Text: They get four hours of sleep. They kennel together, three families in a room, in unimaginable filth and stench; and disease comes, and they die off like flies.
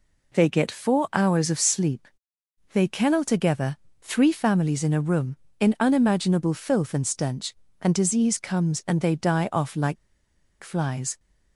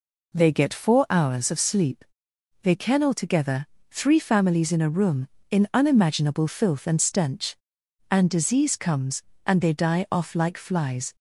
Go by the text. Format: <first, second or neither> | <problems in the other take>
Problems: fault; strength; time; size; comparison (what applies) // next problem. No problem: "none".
second | pauses between "like" and "flies"; noticeable; at 9.9 s; 0.67 s long